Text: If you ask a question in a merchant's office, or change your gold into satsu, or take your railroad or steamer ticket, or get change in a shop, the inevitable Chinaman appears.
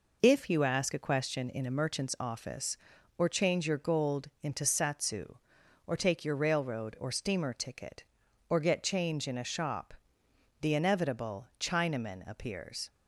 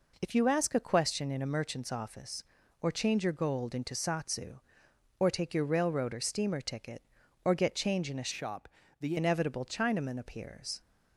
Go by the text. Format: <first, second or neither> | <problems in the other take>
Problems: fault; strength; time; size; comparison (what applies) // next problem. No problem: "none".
first | changes voice from "shop" to "the"; from 8.3 to 9.1 s; 0.8 s long